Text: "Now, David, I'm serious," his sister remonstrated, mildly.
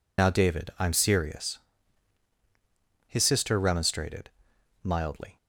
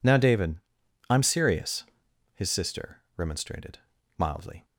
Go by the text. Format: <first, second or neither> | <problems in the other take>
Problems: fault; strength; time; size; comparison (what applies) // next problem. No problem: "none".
second | loses the start of "Now"; at 0.1 s; 55 ms